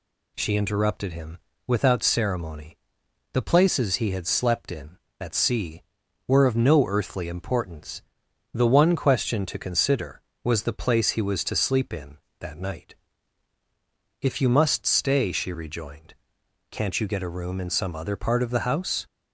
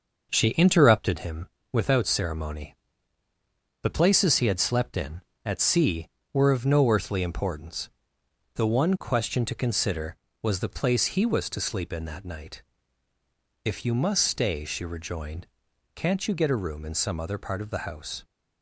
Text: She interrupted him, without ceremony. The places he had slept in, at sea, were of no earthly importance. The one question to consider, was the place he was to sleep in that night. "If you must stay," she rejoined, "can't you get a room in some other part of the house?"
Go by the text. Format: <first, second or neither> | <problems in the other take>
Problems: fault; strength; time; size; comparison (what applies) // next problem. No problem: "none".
first | starts louder than the rest; noticeable; until 1.3 s; 6 dB